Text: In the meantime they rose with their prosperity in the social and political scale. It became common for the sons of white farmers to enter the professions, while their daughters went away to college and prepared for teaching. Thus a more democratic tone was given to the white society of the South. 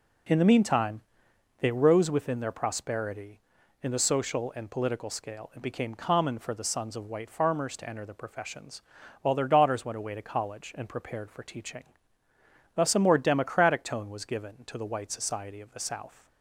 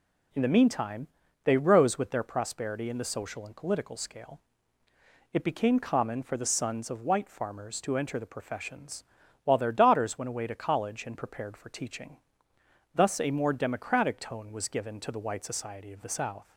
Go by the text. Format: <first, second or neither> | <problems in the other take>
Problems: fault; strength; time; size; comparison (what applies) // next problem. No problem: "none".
second | pauses between "meantime" and "they"; noticeable; at 1.0 s; 0.58 s long; slight in the second // says "within" for "with"; at 2.0 s